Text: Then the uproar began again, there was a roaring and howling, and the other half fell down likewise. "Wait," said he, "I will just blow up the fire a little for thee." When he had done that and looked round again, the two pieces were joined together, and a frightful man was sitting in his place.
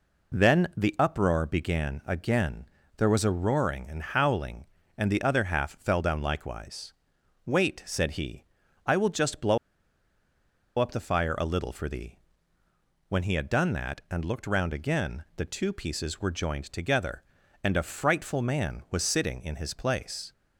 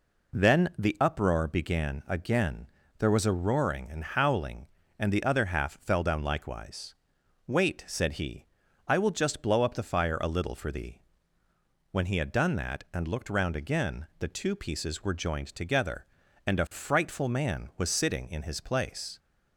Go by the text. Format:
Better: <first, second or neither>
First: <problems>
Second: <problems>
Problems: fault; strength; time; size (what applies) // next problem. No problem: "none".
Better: second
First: pauses between "blow" and "up"; at 9.5 s; 1.2 s long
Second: none